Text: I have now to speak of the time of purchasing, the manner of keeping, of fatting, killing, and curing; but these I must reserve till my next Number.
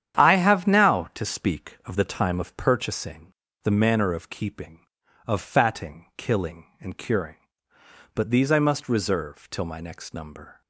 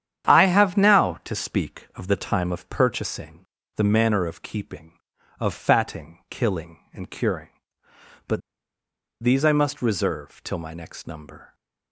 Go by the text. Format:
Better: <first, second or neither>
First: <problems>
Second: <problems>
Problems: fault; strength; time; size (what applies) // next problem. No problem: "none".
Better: first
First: starts louder than the rest; strong; until 1.2 s; 9.5 dB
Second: starts louder than the rest; strong; until 1.3 s; 9.5 dB // pauses between "but" and "these"; noticeable; at 8.4 s; 0.81 s long